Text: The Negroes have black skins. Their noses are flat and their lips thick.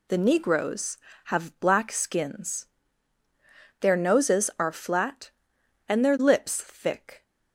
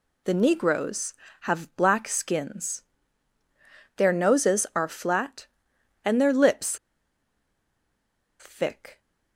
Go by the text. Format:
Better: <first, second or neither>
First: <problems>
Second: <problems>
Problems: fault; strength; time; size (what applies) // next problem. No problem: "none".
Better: first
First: none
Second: pauses between "lips" and "thick"; strong; at 6.7 s; 1.6 s long